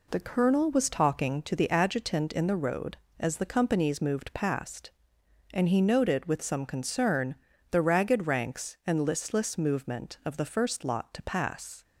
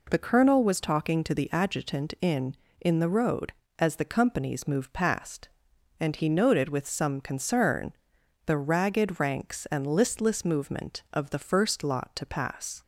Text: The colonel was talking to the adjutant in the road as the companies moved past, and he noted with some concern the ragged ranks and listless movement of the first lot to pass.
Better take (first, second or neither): first